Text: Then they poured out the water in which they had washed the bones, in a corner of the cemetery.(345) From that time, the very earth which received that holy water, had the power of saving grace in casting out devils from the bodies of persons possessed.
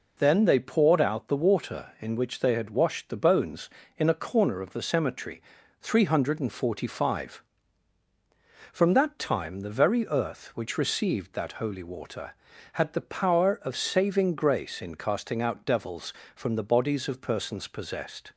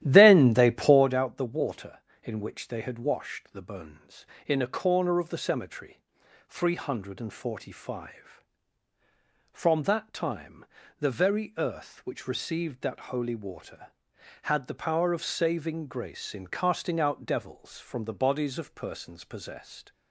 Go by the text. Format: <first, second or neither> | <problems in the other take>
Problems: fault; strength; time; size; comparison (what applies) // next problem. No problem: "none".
first | starts louder than the rest; strong; until 1.1 s; 14.5 dB